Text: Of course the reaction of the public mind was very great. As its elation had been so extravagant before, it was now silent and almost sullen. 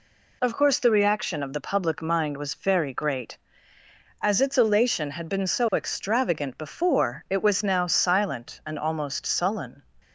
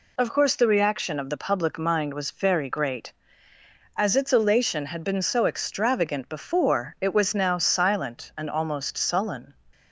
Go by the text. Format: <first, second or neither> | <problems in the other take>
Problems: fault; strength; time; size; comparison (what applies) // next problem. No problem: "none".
neither | none